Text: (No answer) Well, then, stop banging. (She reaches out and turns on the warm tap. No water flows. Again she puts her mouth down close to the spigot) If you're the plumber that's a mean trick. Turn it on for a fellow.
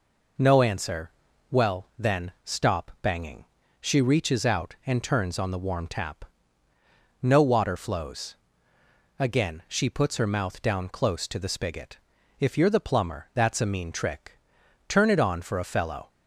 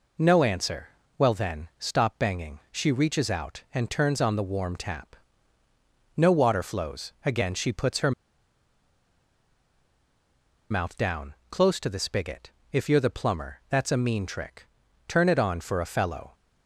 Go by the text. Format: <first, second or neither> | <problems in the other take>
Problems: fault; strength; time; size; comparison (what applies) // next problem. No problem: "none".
first | pauses between "her" and "mouth"; strong; at 8.1 s; 2.5 s long // pauses between "down" and "close"; slight; at 11.3 s; 0.16 s long